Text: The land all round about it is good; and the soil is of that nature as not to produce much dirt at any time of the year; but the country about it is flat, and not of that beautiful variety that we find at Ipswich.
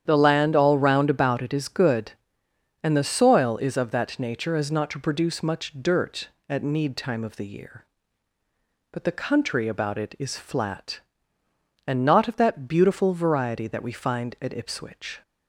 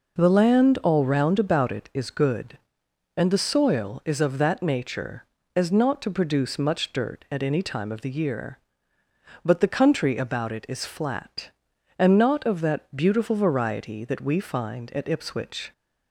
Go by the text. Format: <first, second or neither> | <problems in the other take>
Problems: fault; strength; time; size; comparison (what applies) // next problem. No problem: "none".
second | starts louder than the rest; strong; until 1.0 s; 9 dB // says "need" for "any"; at 6.6 s